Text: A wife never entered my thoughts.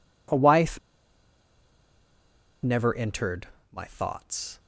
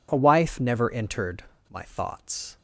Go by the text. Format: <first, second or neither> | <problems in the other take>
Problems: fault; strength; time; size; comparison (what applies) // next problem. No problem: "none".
second | pauses between "wife" and "never"; strong; at 0.7 s; 1.8 s long // pauses between "entered" and "my"; slight; at 3.4 s; 0.24 s long; slight in the second